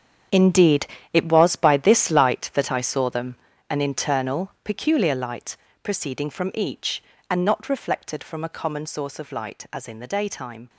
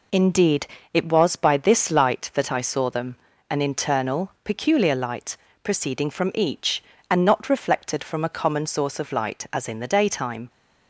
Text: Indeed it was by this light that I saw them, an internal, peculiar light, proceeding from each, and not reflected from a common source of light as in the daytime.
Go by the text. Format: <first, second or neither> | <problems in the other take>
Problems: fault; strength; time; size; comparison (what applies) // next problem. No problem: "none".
second | gets quieter; strong; throughout; 13 dB // pauses between "Indeed" and "it"; slight; at 0.8 s; 0.26 s long; slight in the second